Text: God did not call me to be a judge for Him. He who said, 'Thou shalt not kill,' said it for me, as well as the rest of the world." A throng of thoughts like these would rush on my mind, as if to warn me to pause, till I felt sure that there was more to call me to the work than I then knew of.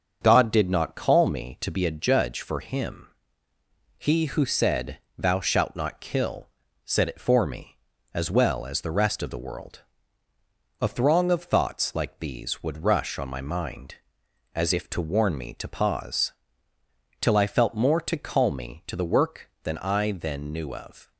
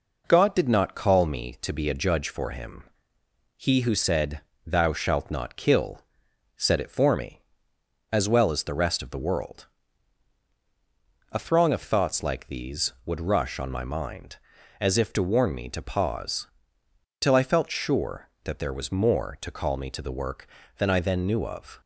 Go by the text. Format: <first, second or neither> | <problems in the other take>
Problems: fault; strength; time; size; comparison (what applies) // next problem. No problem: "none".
second | starts louder than the rest; until 1.2 s; 7 dB // skips "sure that there was"; at 17.7 s